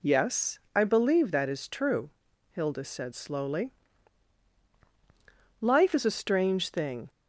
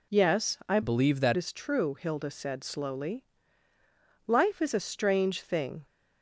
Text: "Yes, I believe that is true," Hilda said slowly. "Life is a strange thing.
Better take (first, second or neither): first